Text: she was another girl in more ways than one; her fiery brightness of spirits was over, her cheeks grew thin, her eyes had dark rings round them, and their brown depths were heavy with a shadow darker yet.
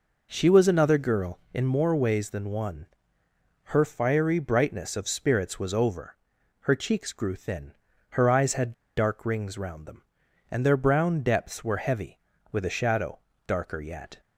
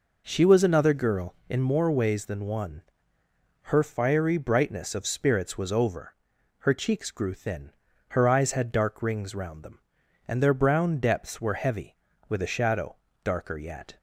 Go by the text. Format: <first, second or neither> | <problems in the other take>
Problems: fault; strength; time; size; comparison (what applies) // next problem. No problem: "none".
second | pauses between "had" and "dark"; slight; at 8.7 s; 0.21 s long // pauses between "shadow" and "darker"; slight; at 13.2 s; 0.26 s long; slight in the second